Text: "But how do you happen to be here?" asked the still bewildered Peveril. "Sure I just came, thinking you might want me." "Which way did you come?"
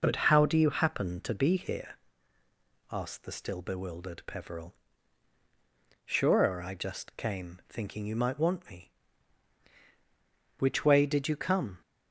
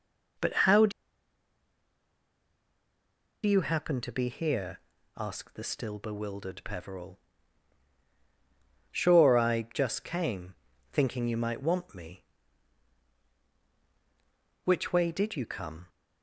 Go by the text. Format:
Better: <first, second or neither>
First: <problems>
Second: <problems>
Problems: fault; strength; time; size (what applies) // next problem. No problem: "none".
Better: first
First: none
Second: pauses between "do" and "you"; strong; at 0.9 s; 2.5 s long